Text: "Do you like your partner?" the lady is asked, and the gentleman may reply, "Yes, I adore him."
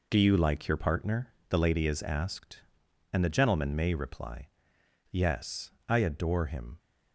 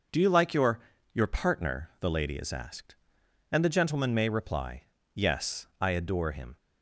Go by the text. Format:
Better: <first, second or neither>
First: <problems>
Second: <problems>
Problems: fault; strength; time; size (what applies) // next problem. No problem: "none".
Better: first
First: none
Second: says "your" twice; at 1.1 s